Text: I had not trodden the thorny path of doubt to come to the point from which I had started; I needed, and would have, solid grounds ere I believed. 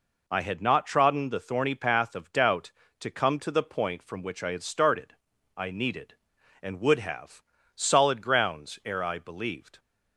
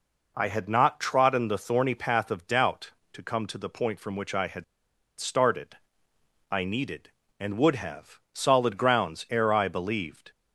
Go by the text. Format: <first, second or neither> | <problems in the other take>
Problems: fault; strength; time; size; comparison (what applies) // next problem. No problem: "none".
first | pauses between "had" and "started"; noticeable; at 4.6 s; 0.56 s long